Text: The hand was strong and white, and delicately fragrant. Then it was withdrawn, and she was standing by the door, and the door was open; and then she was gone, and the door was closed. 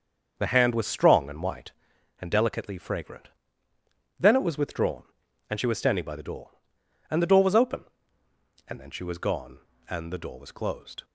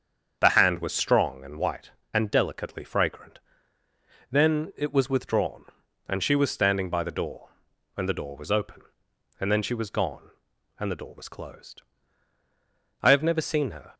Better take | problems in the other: first | starts louder than the rest; strong; until 1.4 s; 7.5 dB; also in the first // goes on to say "I have never seen her"; noticeable; from 13.0 s on; 0.92 s long

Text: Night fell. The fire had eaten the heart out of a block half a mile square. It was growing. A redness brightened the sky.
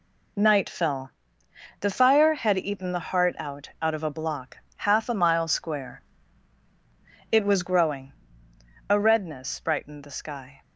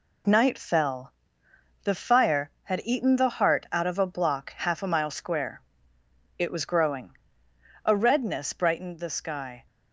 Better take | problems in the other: second | says "out" twice; at 3.8 s // pauses between "block" and "half"; slight; at 4.5 s; 0.20 s long

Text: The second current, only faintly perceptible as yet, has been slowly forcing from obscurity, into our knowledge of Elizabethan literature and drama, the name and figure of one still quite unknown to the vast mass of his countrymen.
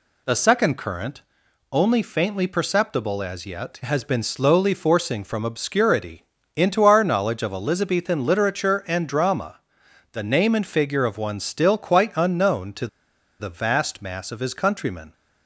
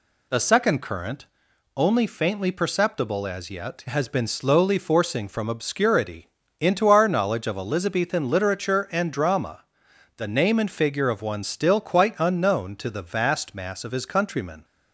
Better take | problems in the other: second | pauses between "to" and "the"; noticeable; at 12.8 s; 0.53 s long

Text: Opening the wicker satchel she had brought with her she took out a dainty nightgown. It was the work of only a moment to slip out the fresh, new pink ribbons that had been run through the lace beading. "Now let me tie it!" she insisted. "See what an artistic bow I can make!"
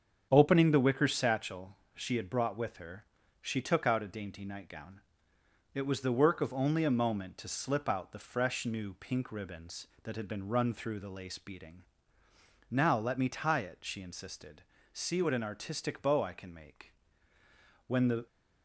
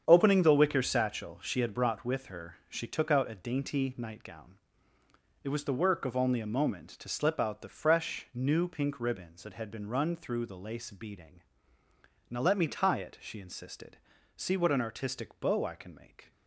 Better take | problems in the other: second | starts louder than the rest; strong; until 1.3 s; 7.5 dB; strong in the second // pauses between "satchel" and "she"; slight; at 1.7 s; 0.18 s long // pauses between "her" and "she"; slight; at 3.0 s; 0.36 s long // goes on to say "When the"; slight; from 17.8 s on; 0.40 s long

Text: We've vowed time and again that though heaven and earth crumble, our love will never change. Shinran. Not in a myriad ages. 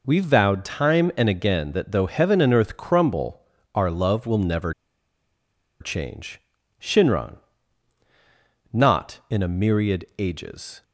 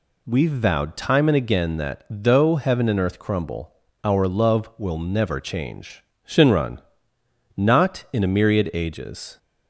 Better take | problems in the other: second | pauses between "never" and "change"; at 4.7 s; 1.0 s long

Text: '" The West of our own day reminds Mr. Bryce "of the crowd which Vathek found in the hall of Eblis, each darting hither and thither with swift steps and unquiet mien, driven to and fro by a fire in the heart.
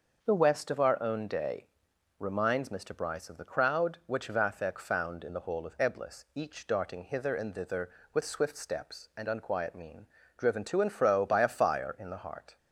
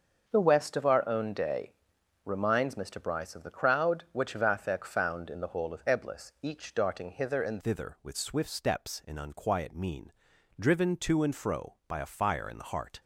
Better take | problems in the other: first | starts louder than the rest; until 1.3 s; 6.5 dB; noticeable in the first // pauses between "day" and "reminds"; noticeable; at 1.7 s; 0.54 s long; noticeable in the first // changes voice at "thither"; from 7.5 s on; 5.5 s long

